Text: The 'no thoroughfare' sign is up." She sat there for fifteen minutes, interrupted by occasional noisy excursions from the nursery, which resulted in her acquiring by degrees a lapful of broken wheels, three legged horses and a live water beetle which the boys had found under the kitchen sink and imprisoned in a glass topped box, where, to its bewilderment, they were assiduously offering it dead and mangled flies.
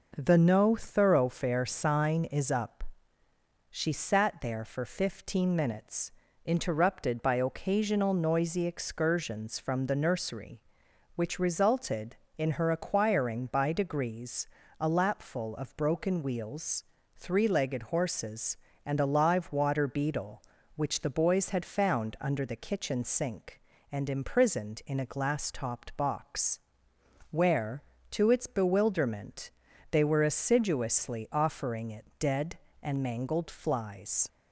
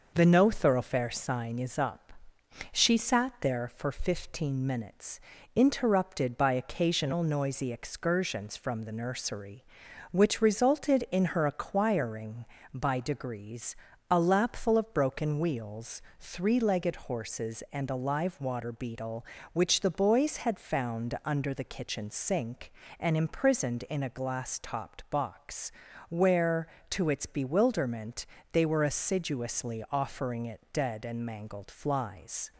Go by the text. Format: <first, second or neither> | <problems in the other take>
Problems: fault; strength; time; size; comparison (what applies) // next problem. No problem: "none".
neither | pauses between "degrees" and "a"; slight; the same in both